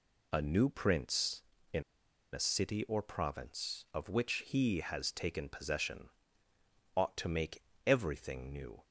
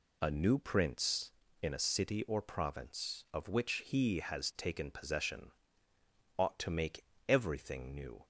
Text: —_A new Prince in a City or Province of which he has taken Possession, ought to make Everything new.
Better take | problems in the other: second | pauses between "in" and "a"; noticeable; at 1.8 s; 0.52 s long // pauses between "make" and "Everything"; slight; at 7.6 s; 0.24 s long; slight in the second

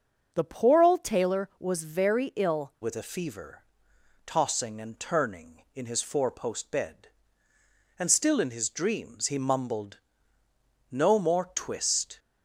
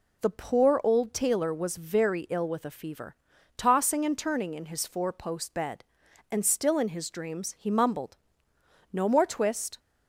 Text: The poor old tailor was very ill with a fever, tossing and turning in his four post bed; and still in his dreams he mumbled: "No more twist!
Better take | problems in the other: second | starts louder than the rest; noticeable; until 1.3 s; 6 dB // changes voice at "with"; from 2.8 s on; 9.3 s long

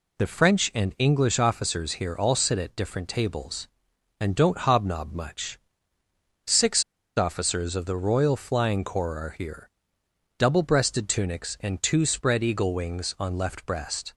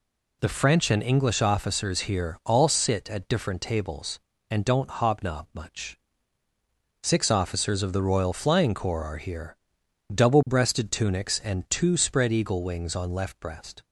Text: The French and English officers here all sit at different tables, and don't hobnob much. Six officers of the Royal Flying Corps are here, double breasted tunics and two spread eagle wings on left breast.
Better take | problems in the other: second | pauses between "Six" and "officers"; at 6.8 s; 0.36 s long

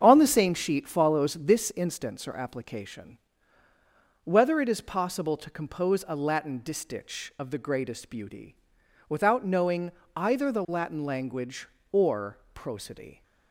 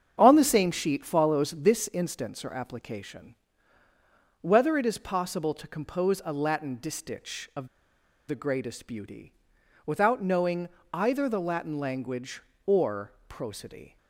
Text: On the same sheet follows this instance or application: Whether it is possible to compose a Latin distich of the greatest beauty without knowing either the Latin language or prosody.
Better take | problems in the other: first | starts louder than the rest; strong; until 1.1 s; 7.5 dB; strong in the first // pauses between "of" and "the"; noticeable; at 7.6 s; 0.60 s long // pauses between "beauty" and "without"; noticeable; at 9.3 s; 0.52 s long; noticeable in the first // pauses between "knowing" and "either"; slight; at 10.6 s; 0.24 s long; slight in the first // pauses between "or" and "prosody"; slight; at 13.1 s; 0.16 s long; slight in the first

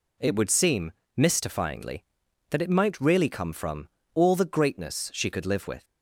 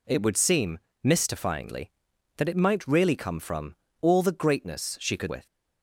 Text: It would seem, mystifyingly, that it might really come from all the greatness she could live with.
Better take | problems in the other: first | pauses between "from" and "all"; slight; at 3.7 s; 0.26 s long; slight in the first // skips "live"; at 5.2 s

